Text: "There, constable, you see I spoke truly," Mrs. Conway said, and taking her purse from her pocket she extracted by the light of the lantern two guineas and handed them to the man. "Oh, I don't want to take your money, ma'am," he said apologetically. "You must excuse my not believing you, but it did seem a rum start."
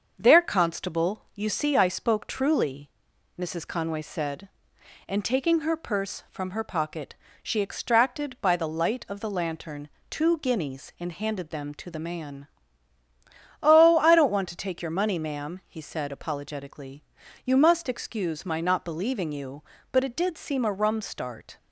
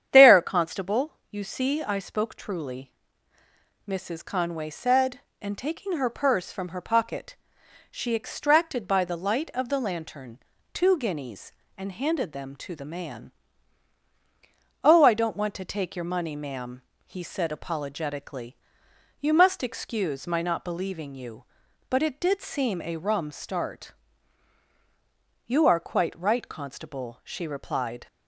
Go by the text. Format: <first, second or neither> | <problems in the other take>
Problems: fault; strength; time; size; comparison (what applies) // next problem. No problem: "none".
first | starts louder than the rest; strong; until 1.1 s; 8.5 dB; also in the first // pauses between "pocket" and "she"; noticeable; at 7.3 s; 0.56 s long; slight in the first // pauses between "lantern" and "two"; slight; at 10.3 s; 0.34 s long; slight in the first // goes on to say "You are quite right constable she replied"; strong; from 25.4 s on; 2.6 s long